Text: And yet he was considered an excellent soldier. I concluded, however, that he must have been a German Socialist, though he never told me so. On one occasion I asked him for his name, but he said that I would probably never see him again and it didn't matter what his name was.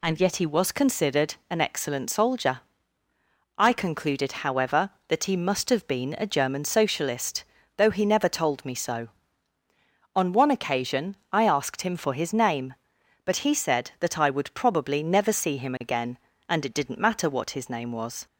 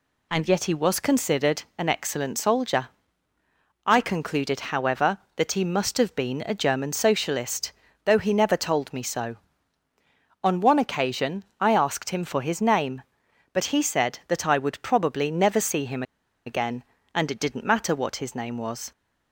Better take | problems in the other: first | pauses between "considered" and "an"; slight; at 1.6 s; 0.16 s long; slight in the first // pauses between "occasion" and "I"; slight; at 11.4 s; 0.16 s long; slight in the first // pauses between "him" and "again"; at 16.0 s; 0.43 s long

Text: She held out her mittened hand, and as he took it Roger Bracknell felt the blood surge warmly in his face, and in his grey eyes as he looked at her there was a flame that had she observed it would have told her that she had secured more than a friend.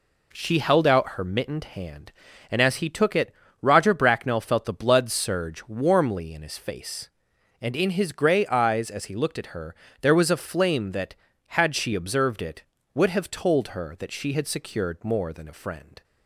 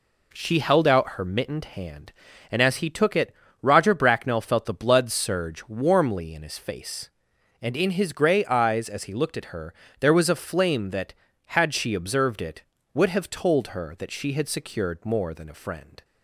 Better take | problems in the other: neither | pauses between "it" and "Roger"; slight; the same in both // pauses between "her" and "there"; slight; the same in both

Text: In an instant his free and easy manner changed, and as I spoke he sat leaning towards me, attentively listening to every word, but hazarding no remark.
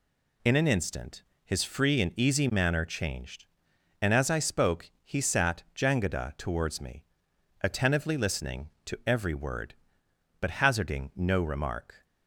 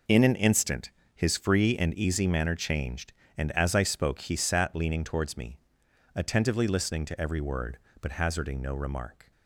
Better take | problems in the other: second | pauses between "instant" and "his"; slight; at 1.2 s; 0.22 s long; slight in the second // says "jangada" for "leaning"; at 5.7 s

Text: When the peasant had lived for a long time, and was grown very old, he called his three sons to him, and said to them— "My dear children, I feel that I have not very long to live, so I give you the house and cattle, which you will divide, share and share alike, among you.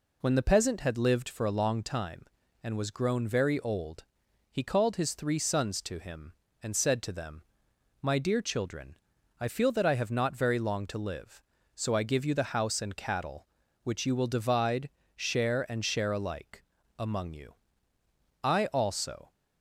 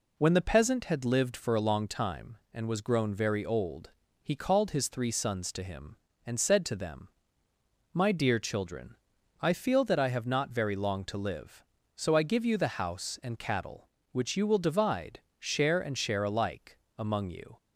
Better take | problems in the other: second | goes on to say "I also"; noticeable; from 18.4 s on; 0.88 s long

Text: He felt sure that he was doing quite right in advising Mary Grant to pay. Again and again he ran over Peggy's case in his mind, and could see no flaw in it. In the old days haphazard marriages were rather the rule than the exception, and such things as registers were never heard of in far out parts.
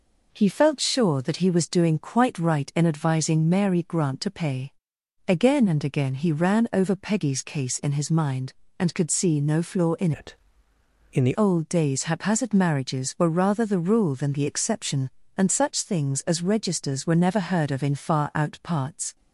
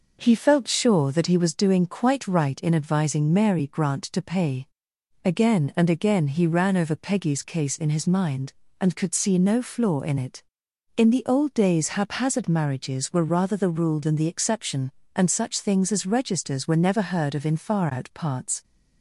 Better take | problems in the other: second | changes voice from "it" to "the"; from 10.1 to 11.3 s; 1.2 s long

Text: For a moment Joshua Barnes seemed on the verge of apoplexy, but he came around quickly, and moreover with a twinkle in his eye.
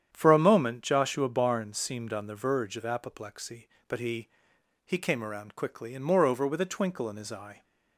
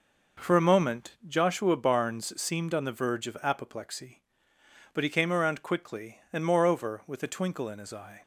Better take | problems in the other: second | starts louder than the rest; strong; until 1.1 s; 9 dB // says "he" twice; at 4.8 s

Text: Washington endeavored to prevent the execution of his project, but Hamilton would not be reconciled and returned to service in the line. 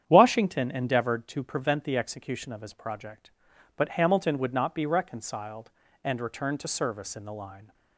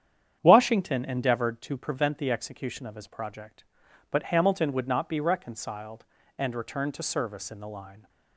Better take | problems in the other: neither | starts louder than the rest; strong; the same in both

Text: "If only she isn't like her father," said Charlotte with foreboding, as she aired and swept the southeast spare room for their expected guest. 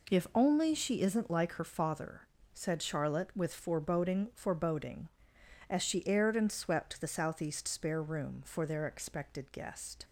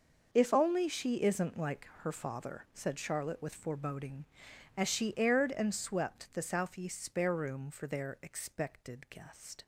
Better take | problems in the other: second | says "foreboding" twice; at 4.3 s

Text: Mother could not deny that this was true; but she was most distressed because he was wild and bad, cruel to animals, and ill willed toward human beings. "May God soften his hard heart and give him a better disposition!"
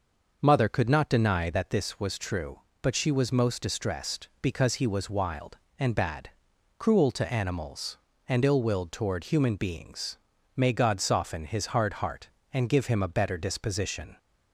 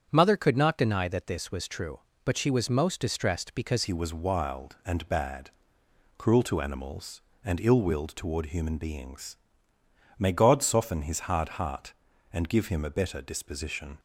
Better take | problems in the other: first | starts louder than the rest; strong; until 1.1 s; 8 dB // changes voice at "he"; from 3.8 s on; 10.1 s long

